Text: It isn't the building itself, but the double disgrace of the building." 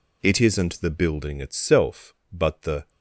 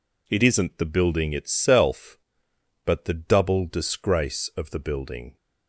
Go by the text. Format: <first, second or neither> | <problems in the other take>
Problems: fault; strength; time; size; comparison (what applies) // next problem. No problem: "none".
second | stops before "double disgrace of the building"; at 2.8 s